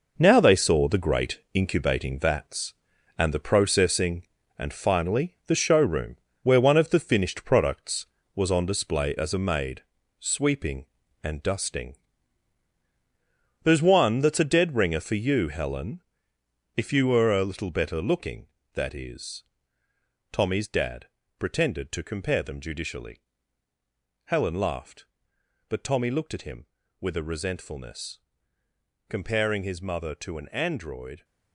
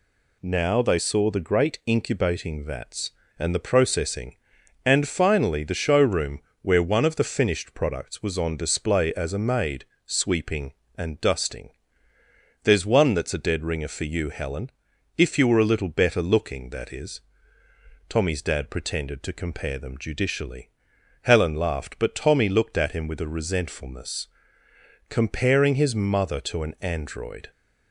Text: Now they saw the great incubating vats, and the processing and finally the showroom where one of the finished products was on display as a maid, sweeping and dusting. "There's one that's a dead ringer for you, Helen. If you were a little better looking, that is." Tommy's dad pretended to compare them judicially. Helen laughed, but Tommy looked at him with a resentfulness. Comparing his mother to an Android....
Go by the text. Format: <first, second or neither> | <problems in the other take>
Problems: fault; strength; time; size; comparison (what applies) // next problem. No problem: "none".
second | gets quieter; strong; throughout; 9 dB // pauses between "showroom" and "where"; slight; at 6.1 s; 0.28 s long; slight in the second // pauses between "dad" and "pretended"; slight; at 21.0 s; 0.30 s long